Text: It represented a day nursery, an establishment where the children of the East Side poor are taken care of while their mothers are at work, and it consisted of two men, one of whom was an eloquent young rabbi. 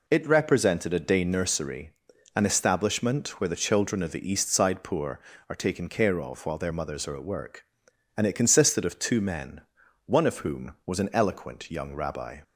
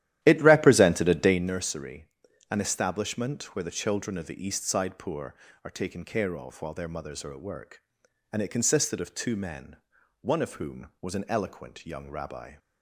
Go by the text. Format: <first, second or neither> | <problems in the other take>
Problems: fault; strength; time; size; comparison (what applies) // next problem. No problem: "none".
first | starts louder than the rest; strong; until 1.5 s; 12.5 dB